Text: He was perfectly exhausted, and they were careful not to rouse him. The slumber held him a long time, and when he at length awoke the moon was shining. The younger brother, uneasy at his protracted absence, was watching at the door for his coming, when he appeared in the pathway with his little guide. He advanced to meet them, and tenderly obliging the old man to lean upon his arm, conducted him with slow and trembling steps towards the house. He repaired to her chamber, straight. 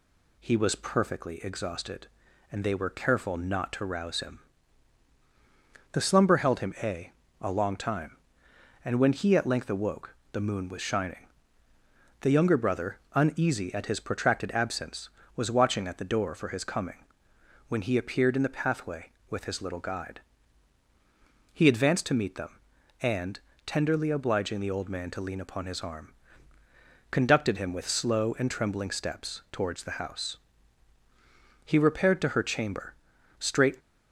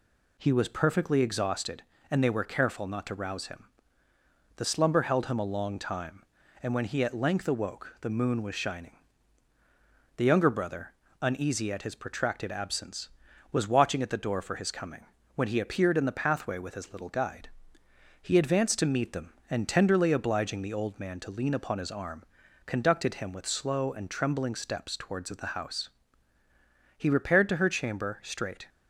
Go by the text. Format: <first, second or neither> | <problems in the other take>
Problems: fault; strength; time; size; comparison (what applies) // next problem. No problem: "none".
second | says "a" twice; at 7.3 s // pauses between "awoke" and "the"; slight; at 10.1 s; 0.18 s long // pauses between "and" and "tenderly"; slight; at 23.3 s; 0.26 s long